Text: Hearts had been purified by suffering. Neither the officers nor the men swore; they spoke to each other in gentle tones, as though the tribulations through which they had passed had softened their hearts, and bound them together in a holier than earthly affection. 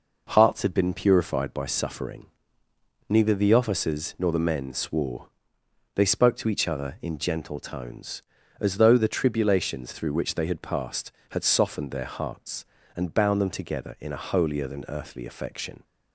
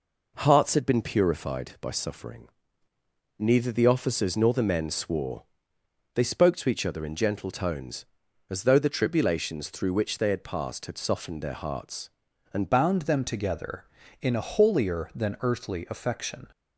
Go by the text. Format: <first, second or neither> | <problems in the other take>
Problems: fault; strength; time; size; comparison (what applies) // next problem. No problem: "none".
first | changes voice at "bound"; from 12.7 s on; 3.7 s long